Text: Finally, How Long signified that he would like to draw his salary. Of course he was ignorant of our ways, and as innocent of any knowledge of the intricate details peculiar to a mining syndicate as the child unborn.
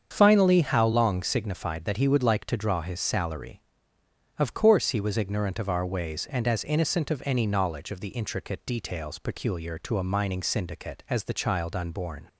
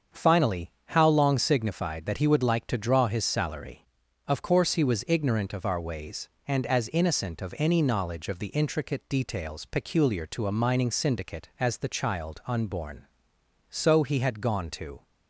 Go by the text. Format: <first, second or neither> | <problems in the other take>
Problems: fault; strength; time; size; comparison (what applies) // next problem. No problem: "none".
first | starts louder than the rest; strong; until 1.2 s; 7 dB; strong in the first // goes on to say "So he had gone to"; from 13.7 s on; 1.3 s long